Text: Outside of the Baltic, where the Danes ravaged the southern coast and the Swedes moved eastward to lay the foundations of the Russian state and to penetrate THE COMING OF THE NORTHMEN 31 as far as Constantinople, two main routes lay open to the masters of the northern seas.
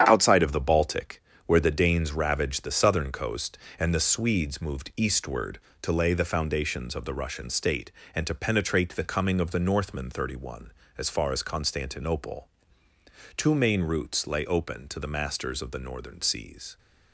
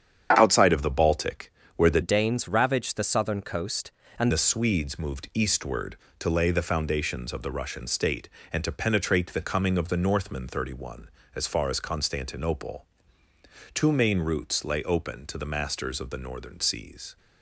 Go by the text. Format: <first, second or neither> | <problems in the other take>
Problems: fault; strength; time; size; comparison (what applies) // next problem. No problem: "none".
first | starts louder than the rest; strong; until 1.3 s; 8 dB; strong in the first // changes voice from "Danes" to "and"; from 2.0 to 4.3 s; 2.3 s long